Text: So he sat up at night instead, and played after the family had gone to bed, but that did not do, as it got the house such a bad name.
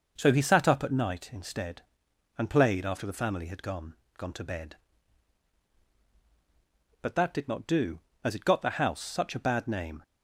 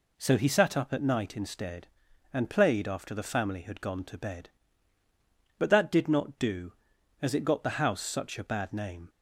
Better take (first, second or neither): second